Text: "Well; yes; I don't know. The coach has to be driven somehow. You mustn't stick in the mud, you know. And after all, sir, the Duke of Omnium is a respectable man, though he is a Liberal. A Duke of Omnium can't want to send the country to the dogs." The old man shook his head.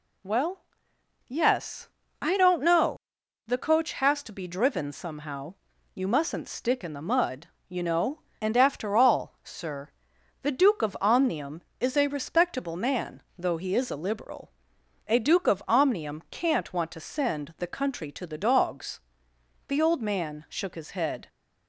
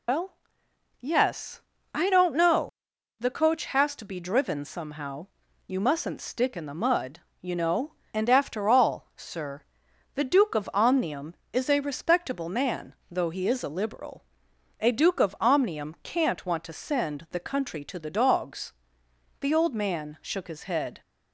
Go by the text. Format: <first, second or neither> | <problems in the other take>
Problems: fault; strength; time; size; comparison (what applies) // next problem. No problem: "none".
first | loses the start of "Well"; at 0.0 s; 140 ms